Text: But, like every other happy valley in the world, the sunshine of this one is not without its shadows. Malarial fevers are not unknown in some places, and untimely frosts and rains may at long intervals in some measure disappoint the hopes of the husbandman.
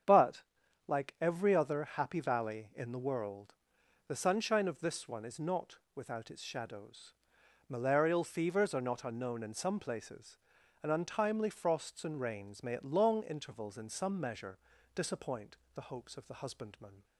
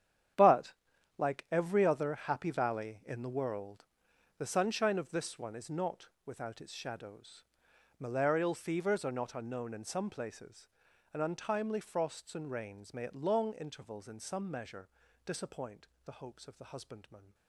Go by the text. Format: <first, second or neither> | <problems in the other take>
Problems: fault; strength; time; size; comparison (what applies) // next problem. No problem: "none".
first | gets quieter; strong; throughout; 13.5 dB // starts louder than the rest; strong; until 1.9 s; 10 dB; strong in the first // pauses between "not" and "without"; slight; at 6.0 s; 0.18 s long; slight in the first // pauses between "measure" and "disappoint"; at 14.8 s; 0.38 s long; also in the first // pauses between "disappoint" and "the"; slight; at 15.8 s; 0.20 s long; slight in the first